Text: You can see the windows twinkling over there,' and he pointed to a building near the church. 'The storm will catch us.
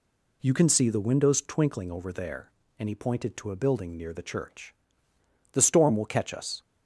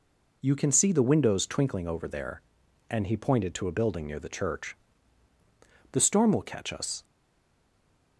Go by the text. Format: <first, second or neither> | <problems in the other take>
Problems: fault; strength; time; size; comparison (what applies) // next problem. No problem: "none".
first | stays silent after the last word; noticeable; from 7.0 s on; 1.1 s long